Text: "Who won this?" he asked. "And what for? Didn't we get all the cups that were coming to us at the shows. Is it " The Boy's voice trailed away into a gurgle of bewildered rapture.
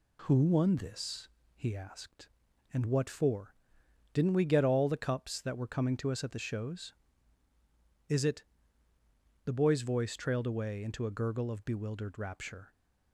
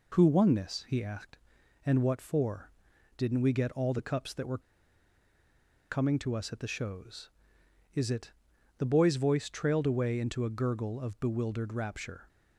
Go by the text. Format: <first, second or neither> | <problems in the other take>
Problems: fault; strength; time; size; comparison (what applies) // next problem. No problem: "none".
first | pauses between "were" and "coming"; strong; at 4.5 s; 1.3 s long